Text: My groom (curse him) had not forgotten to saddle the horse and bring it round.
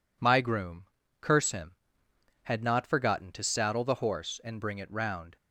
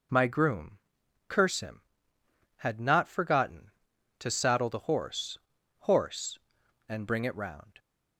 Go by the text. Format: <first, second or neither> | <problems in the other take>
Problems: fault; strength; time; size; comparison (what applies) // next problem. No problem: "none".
first | says "horse" twice; at 5.8 s